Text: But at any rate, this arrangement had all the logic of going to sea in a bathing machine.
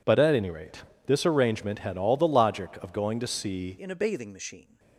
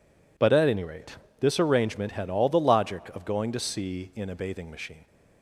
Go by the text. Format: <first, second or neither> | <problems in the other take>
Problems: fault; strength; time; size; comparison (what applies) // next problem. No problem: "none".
second | changes voice at "in"; from 3.7 s on; 1.0 s long